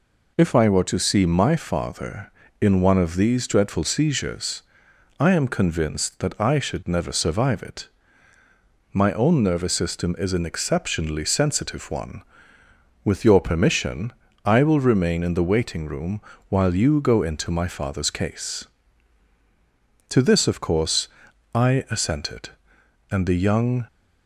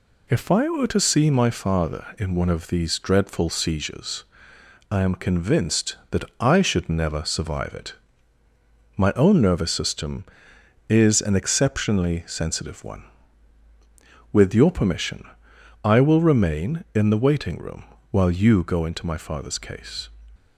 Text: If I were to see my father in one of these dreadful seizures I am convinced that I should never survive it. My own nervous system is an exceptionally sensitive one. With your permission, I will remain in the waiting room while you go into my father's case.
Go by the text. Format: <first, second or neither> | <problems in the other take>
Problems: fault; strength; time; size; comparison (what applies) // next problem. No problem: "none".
second | pauses between "seizures" and "I"; noticeable; at 4.6 s; 0.56 s long; noticeable in the second // pauses between "room" and "while"; slight; at 16.2 s; 0.28 s long; slight in the second // goes on to say "To this of course I assented and the young"; strong; from 20.1 s on; 3.7 s long